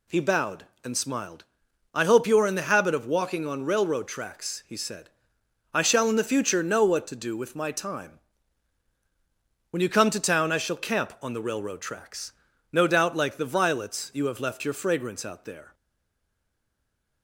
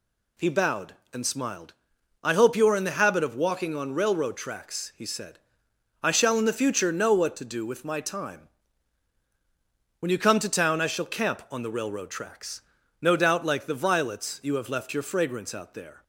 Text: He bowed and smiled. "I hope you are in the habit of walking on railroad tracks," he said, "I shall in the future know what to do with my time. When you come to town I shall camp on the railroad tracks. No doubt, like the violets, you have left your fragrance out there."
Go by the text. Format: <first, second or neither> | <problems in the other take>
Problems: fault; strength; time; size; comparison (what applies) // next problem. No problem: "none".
second | stays silent after the last word; noticeable; from 15.7 s on; 1.5 s long